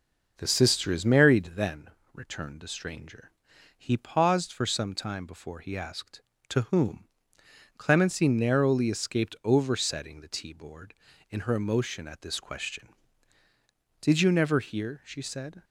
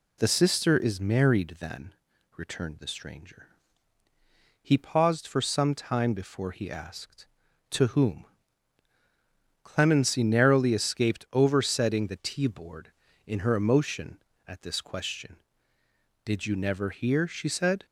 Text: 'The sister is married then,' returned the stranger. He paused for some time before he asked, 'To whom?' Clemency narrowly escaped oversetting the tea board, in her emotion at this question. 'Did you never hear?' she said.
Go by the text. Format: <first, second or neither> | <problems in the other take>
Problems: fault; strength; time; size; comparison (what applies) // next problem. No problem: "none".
neither | none